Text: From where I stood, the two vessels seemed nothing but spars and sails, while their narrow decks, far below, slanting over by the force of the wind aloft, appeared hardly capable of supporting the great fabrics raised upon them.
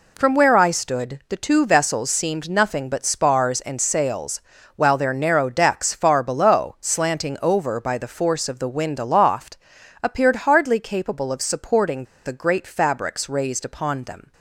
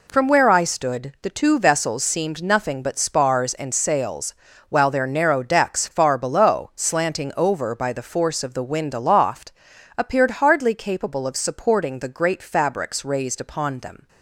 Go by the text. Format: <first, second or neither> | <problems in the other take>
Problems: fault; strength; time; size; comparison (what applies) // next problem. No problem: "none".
second | pauses between "supporting" and "the"; slight; at 12.0 s; 0.20 s long